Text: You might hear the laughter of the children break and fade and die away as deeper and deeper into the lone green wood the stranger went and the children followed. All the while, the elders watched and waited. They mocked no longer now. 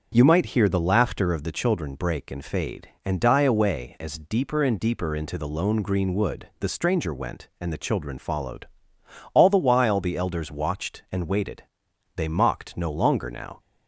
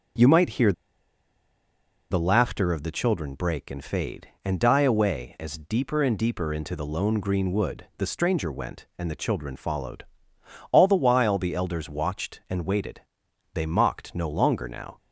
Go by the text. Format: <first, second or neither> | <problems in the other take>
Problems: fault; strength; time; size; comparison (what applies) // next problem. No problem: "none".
first | starts louder than the rest; strong; until 2.5 s; 7 dB; also in the first // pauses between "hear" and "the"; strong; at 0.7 s; 1.3 s long